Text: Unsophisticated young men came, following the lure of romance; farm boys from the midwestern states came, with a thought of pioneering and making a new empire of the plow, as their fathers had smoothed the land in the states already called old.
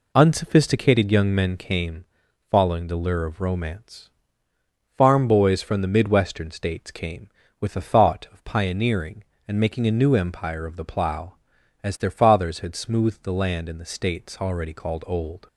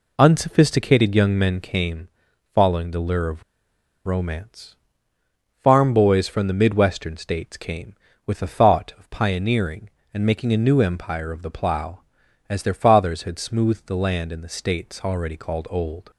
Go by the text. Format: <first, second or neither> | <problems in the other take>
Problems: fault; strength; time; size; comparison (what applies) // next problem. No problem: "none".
first | pauses between "of" and "romance"; noticeable; at 3.4 s; 0.65 s long